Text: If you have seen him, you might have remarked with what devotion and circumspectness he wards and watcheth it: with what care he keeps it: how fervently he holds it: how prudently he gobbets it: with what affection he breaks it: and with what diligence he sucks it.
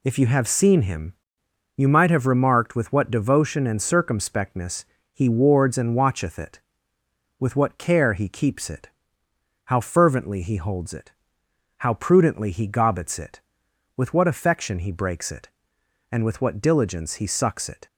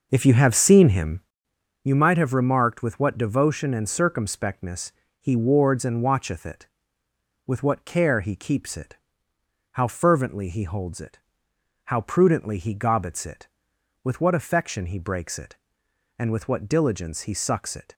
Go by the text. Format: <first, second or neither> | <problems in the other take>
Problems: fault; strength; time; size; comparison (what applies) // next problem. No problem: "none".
first | starts louder than the rest; noticeable; until 1.3 s; 5.5 dB // pauses between "circumspectness" and "he"; slight; at 4.9 s; 0.28 s long; slight in the first